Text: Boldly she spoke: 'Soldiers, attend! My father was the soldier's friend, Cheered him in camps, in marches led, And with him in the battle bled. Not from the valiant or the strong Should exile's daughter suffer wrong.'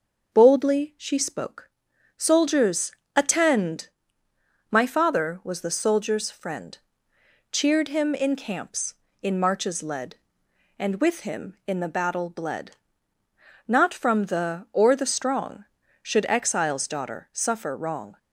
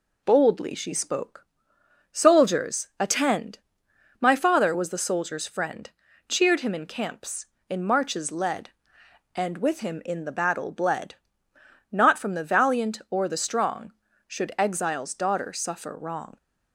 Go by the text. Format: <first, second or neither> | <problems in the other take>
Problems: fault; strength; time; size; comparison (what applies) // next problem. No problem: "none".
second | starts louder than the rest; until 1.3 s; 6 dB // skips "valiant"; at 14.6 s